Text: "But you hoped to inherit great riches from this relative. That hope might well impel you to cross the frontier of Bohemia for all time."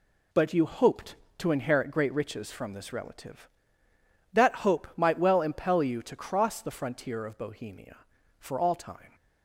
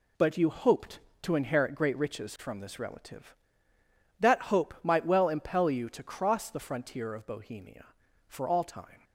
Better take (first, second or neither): neither